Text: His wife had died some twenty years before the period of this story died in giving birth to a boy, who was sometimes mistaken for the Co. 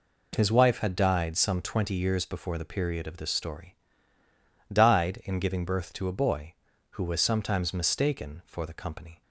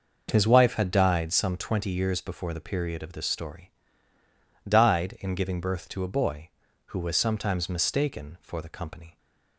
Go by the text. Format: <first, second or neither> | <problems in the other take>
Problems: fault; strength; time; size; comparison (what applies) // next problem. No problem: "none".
first | starts louder than the rest; noticeable; until 1.4 s; 6 dB // pauses between "story" and "died"; noticeable; at 3.7 s; 0.96 s long; noticeable in the first